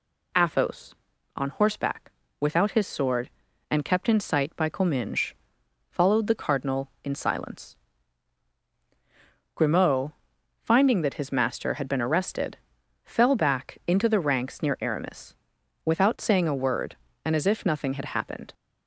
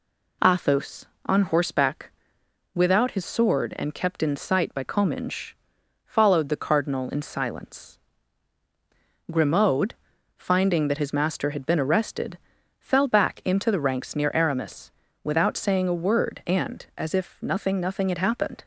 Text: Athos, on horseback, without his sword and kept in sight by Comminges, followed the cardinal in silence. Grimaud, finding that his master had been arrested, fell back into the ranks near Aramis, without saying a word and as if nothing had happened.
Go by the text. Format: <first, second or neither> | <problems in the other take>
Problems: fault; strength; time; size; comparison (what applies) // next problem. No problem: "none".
first | says "nothing" twice; at 17.7 s